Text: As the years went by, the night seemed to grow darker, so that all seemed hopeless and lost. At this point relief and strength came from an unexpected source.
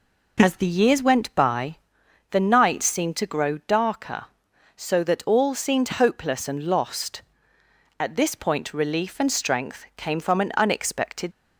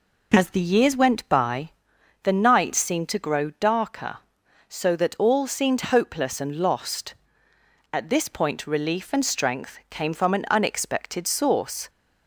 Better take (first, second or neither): second